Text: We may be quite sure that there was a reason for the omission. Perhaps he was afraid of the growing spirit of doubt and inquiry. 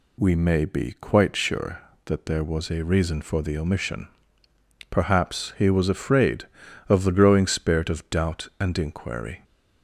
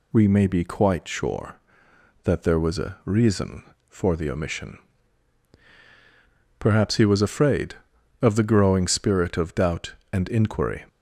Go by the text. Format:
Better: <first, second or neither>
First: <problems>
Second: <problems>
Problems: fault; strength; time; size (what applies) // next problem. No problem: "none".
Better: neither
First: none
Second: none